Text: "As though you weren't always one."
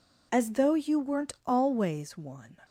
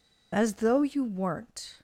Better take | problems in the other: first | stops before "always one"; at 1.7 s

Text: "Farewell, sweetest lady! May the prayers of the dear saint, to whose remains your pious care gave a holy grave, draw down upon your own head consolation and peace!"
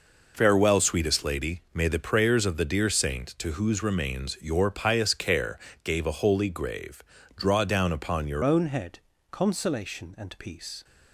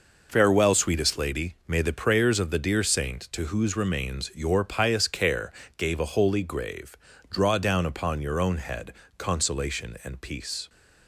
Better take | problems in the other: second | pauses between "care" and "gave"; slight; at 5.5 s; 0.26 s long; slight in the second // changes voice at "own"; from 8.4 s on; 2.4 s long // pauses between "head" and "consolation"; slight; at 8.9 s; 0.32 s long; slight in the second

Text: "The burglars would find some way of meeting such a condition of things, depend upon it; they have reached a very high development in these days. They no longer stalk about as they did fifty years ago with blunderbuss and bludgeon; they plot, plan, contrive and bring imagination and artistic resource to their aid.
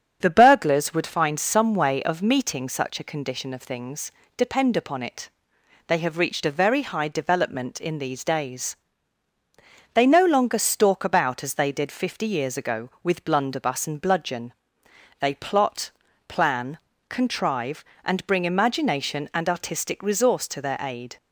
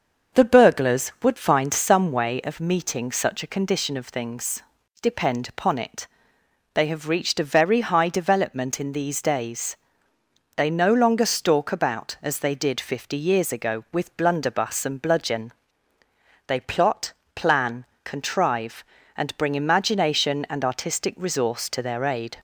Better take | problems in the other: neither | starts louder than the rest; the same in both

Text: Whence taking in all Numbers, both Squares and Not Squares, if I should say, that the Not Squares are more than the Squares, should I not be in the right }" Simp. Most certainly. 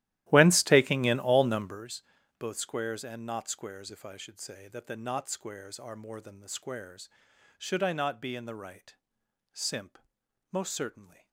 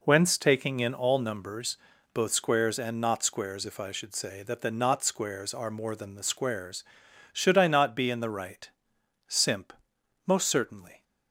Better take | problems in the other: second | starts louder than the rest; strong; until 1.9 s; 14.5 dB

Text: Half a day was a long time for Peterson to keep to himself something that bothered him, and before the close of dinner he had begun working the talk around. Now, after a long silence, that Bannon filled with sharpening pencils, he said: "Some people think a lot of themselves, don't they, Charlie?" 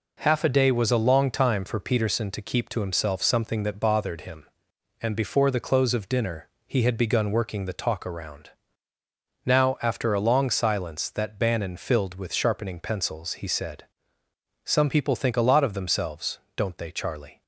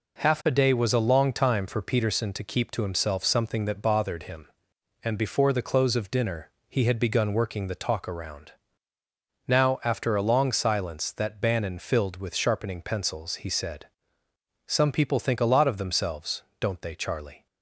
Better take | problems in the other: neither | pauses between "dinner" and "he"; slight; the same in both

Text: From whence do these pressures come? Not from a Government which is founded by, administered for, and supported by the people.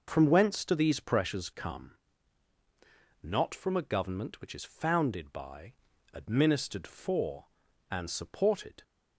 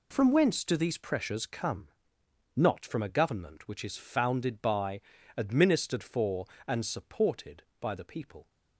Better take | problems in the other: second | stops before "by the people"; at 8.8 s

